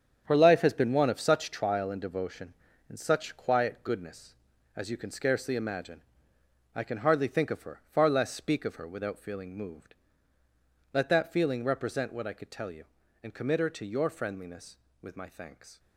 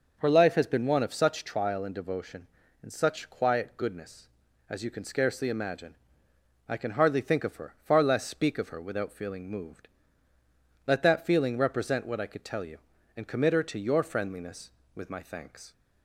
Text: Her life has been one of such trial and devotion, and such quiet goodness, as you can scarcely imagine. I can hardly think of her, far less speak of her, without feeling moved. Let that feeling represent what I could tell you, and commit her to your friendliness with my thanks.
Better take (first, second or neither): second